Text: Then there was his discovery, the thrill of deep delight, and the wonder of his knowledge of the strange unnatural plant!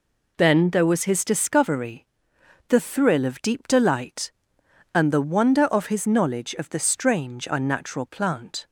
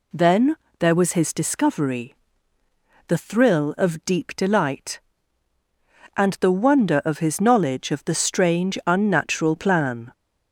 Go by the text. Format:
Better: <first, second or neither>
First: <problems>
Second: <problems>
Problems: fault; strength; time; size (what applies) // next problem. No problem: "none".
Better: first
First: none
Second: pauses between "Then" and "there"; slight; at 0.5 s; 0.24 s long // says "plan" for "plant"; at 9.5 s